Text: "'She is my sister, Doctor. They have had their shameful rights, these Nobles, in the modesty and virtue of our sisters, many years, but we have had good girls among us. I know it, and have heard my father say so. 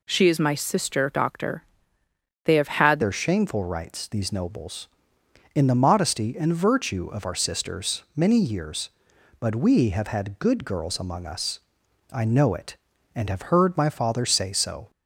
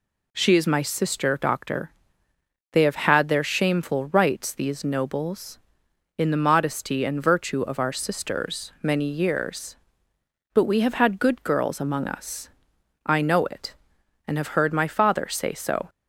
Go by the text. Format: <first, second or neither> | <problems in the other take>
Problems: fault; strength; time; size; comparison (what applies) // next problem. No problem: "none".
second | changes voice at "their"; from 3.0 s on; 11.8 s long